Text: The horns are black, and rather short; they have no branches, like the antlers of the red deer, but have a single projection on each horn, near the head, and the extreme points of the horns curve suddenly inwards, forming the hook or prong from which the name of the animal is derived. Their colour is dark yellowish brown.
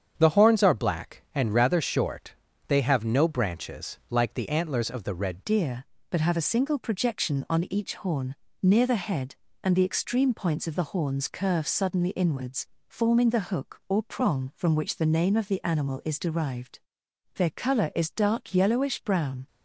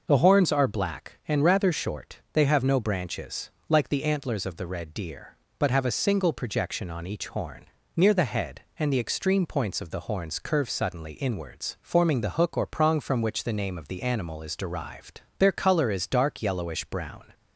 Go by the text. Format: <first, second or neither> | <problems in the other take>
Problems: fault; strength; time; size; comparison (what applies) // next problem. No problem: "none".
second | starts louder than the rest; strong; until 1.1 s; 8 dB // changes voice at "deer"; from 5.4 s on; 14.0 s long